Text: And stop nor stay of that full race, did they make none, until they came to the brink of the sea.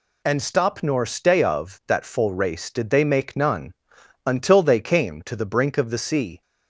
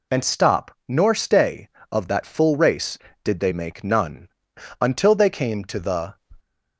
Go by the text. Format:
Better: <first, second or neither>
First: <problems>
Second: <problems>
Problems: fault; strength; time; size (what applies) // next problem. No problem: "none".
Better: first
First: none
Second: stops before "brink of the sea"; at 6.3 s